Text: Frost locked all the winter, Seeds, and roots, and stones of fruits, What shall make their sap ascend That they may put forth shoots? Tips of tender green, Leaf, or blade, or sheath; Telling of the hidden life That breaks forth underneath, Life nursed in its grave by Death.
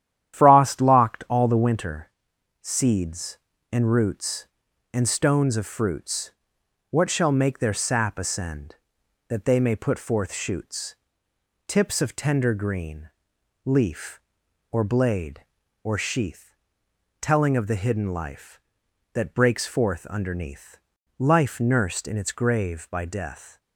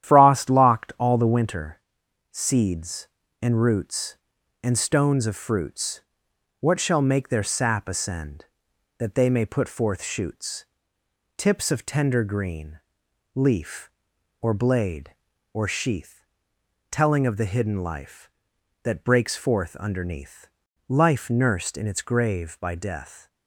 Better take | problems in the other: neither | starts louder than the rest; strong; the same in both

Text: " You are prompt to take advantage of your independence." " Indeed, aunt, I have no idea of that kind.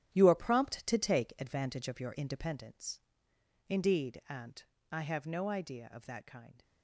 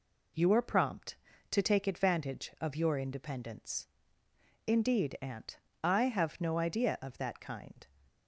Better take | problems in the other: second | gets quieter; strong; throughout; 11 dB

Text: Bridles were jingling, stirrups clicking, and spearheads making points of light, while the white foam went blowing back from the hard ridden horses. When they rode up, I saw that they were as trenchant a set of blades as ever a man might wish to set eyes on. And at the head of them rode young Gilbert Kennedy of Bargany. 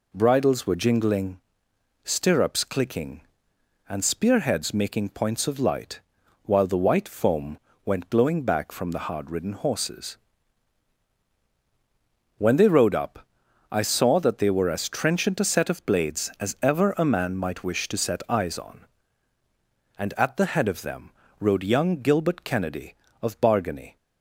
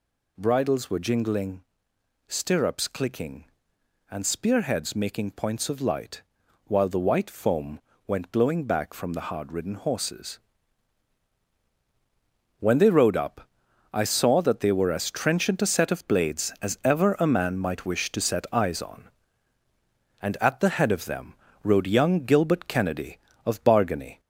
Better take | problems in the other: first | gets louder; slight; throughout; 3.5 dB // pauses between "foam" and "went"; slight; at 7.7 s; 0.28 s long; slight in the first // pauses between "them" and "rode"; slight; at 21.3 s; 0.28 s long; slight in the first

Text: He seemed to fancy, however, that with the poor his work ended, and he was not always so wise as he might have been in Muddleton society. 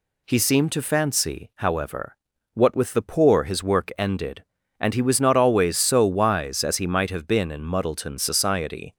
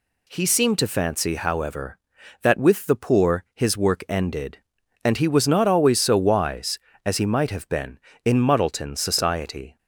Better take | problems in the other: second | says "what" for "that"; at 2.5 s

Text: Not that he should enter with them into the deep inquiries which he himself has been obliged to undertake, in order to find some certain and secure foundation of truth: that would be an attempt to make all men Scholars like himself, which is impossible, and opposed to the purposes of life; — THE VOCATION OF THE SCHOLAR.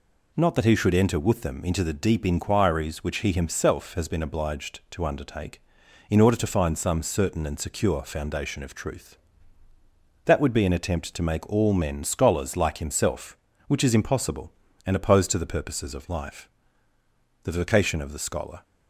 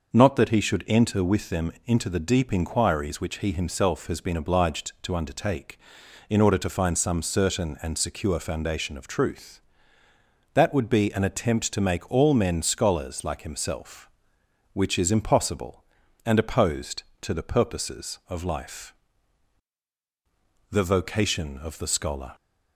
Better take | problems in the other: neither | none

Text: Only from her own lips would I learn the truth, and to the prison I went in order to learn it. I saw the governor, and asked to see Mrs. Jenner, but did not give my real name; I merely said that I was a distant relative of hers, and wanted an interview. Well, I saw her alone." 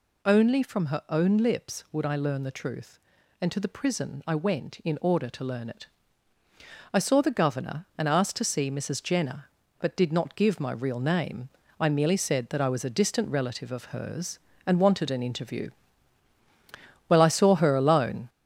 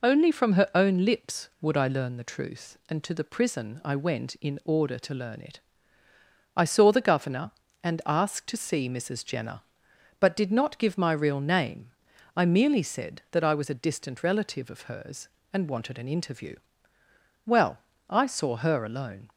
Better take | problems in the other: second | gets louder; noticeable; throughout; 5 dB

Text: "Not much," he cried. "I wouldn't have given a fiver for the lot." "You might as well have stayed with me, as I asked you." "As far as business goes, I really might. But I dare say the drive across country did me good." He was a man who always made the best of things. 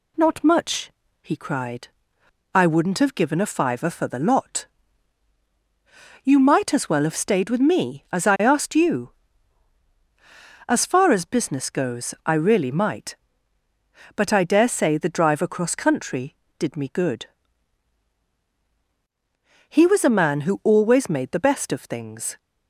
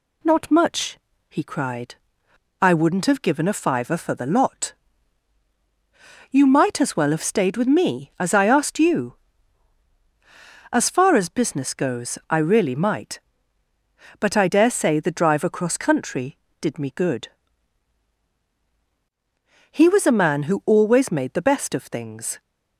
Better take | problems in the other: neither | none

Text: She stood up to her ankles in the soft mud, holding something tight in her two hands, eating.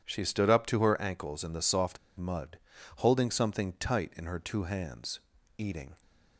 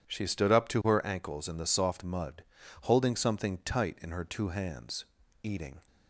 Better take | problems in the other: second | pauses between "soft" and "mud"; slight; at 1.9 s; 0.20 s long

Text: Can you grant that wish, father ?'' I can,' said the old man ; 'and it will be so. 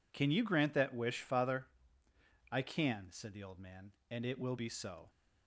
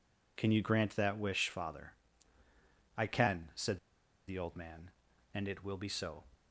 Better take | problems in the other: first | pauses between "said" and "the"; noticeable; at 3.7 s; 0.50 s long

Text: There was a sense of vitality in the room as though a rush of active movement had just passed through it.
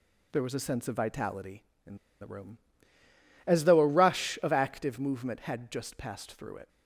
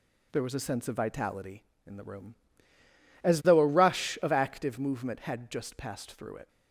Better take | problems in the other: second | pauses between "in" and "the"; slight; at 1.9 s; 0.24 s long

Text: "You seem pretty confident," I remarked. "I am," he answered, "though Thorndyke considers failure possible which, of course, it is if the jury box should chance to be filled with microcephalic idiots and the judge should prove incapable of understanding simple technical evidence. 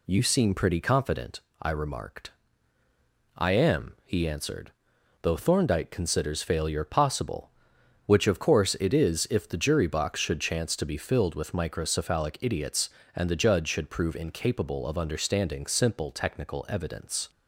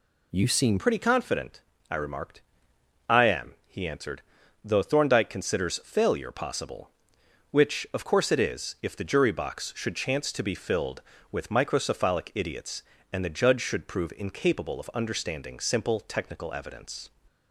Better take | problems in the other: first | changes voice at "pretty"; from 0.7 s on; 16.4 s long

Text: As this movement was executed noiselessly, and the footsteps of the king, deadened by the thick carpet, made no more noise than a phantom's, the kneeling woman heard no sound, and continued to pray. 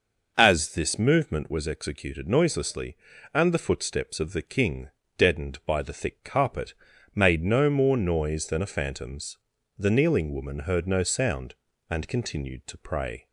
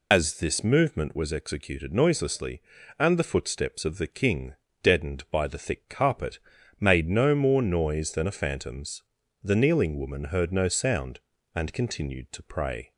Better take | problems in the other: first | loses the start of "As"; at 0.1 s; 90 ms

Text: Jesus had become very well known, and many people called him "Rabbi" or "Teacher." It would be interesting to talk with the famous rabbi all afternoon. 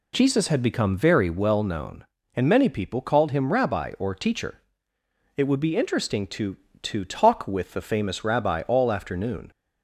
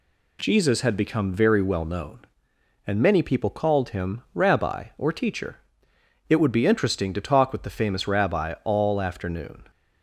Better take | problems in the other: second | says "to" twice; at 6.8 s

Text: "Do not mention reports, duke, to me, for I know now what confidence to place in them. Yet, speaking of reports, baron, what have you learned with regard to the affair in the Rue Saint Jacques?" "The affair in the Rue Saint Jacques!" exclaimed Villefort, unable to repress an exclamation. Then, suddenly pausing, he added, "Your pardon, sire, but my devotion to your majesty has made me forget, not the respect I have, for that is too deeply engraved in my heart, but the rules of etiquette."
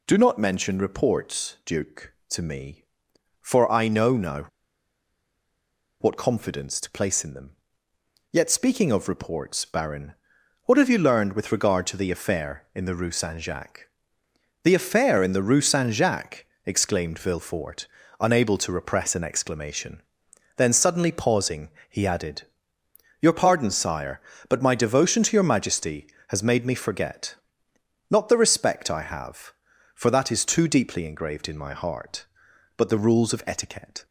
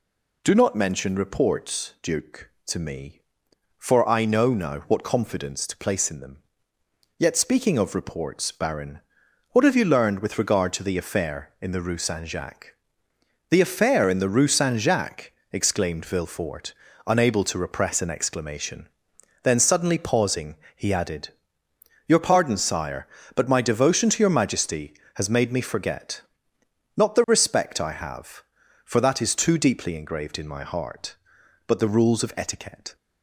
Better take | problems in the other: second | pauses between "now" and "what"; strong; at 4.4 s; 1.5 s long

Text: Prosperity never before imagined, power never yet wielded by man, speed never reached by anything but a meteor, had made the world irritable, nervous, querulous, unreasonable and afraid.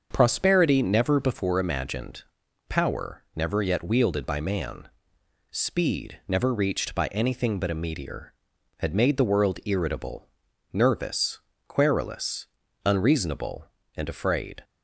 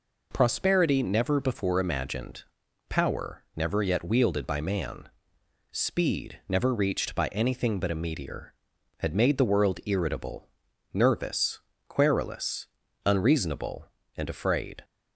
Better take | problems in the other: second | starts louder than the rest; until 1.4 s; 6.5 dB

